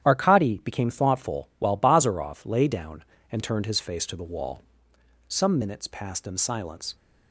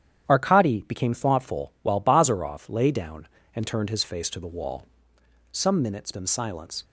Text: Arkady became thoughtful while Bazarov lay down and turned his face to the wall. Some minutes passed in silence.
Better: first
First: starts louder than the rest; strong; until 1.1 s; 10.5 dB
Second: starts louder than the rest; strong; until 1.3 s; 9.5 dB // skips "passed"; at 6.1 s

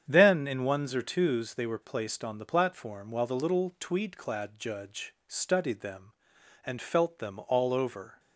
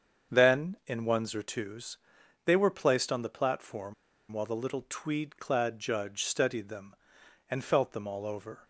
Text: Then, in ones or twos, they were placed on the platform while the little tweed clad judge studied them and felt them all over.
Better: first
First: starts louder than the rest; strong; until 1.0 s; 8 dB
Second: starts louder than the rest; strong; until 1.4 s; 7 dB // pauses between "platform" and "while"; at 3.9 s; 0.37 s long

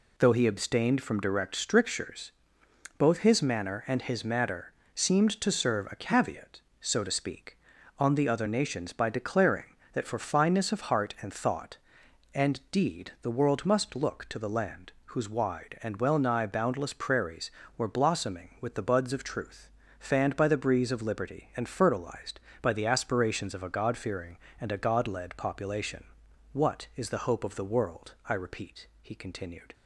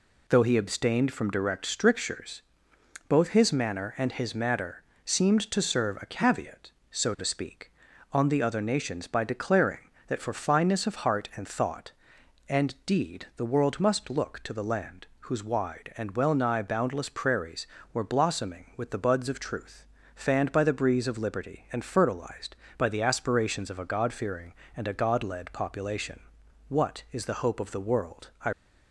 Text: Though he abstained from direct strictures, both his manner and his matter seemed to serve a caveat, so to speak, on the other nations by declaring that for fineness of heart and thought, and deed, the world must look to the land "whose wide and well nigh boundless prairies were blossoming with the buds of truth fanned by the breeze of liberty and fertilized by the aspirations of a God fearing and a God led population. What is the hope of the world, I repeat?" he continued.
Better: first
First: pauses between "matter" and "seemed"; slight; at 4.7 s; 0.22 s long // pauses between "truth" and "fanned"; slight; at 19.6 s; 0.30 s long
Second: pauses between "matter" and "seemed"; slight; at 4.8 s; 0.22 s long // pauses between "truth" and "fanned"; slight; at 19.8 s; 0.30 s long // stops before "repeat he continued"; at 28.5 s

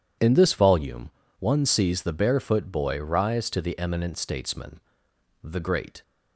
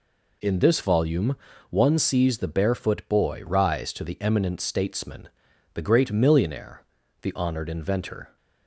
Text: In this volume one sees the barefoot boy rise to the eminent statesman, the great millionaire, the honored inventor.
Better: second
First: pauses between "volume" and "one"; slight; at 1.1 s; 0.28 s long // stops before "millionaire the honored inventor"; at 6.0 s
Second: pauses between "volume" and "one"; slight; at 1.3 s; 0.34 s long

